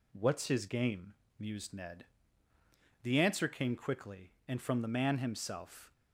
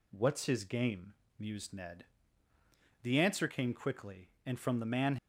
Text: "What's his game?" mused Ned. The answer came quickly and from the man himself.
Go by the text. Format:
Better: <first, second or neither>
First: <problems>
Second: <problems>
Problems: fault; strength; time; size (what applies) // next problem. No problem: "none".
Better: first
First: none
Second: stops before "himself"; at 5.1 s